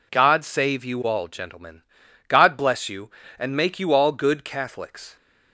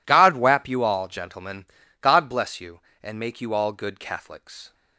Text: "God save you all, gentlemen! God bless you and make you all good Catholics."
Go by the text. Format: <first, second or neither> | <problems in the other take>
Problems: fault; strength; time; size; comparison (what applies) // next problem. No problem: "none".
first | says "wap" for "save"; at 0.3 s